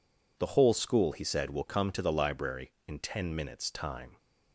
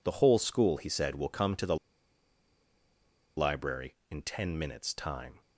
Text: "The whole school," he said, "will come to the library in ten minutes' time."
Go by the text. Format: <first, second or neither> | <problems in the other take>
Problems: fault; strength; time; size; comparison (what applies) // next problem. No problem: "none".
first | pauses between "the" and "library"; strong; at 1.7 s; 1.6 s long